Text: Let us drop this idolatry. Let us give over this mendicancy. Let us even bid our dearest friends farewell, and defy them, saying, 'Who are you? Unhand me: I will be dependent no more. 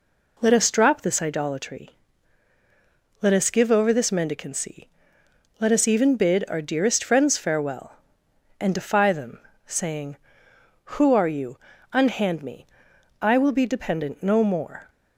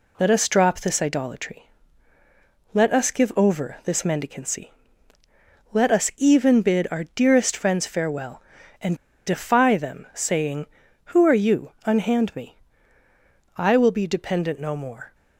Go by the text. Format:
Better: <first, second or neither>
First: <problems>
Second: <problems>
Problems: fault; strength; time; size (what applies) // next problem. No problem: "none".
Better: first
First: none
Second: pauses between "and" and "defy"; slight; at 8.9 s; 0.31 s long